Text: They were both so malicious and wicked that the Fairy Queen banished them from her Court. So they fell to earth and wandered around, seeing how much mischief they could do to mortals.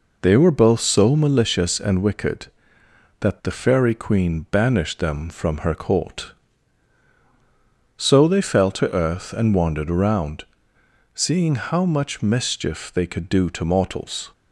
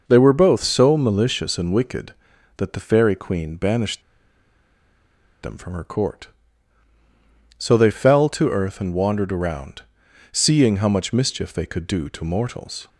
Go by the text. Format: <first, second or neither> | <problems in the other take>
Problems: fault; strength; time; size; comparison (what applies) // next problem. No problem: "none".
first | pauses between "banished" and "them"; strong; at 4.0 s; 1.4 s long